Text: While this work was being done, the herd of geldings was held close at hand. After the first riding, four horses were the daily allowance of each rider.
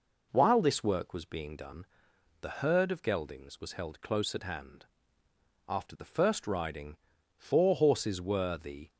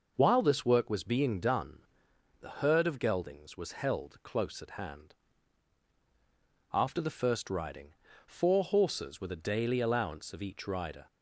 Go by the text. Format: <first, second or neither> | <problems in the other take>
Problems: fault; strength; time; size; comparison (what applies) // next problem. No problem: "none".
second | stops before "daily allowance of each rider"; at 8.8 s